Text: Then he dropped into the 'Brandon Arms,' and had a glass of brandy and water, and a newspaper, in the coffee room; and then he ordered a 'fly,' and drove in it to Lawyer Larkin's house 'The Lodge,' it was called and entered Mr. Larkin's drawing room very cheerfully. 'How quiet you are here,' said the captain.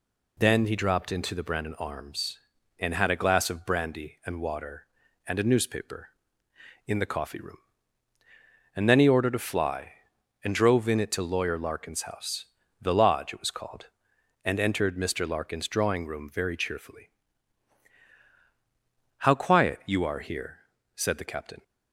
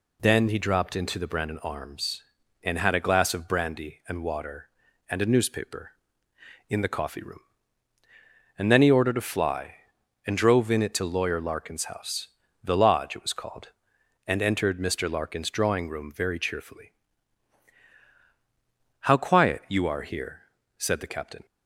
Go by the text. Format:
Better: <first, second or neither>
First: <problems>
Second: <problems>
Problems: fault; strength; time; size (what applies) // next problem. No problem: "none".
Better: neither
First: pauses between "house" and "The"; at 12.4 s; 0.38 s long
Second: pauses between "house" and "The"; at 12.2 s; 0.38 s long